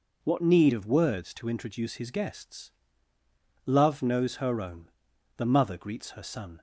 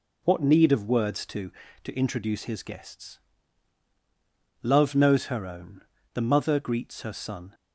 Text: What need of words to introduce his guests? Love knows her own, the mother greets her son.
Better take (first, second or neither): first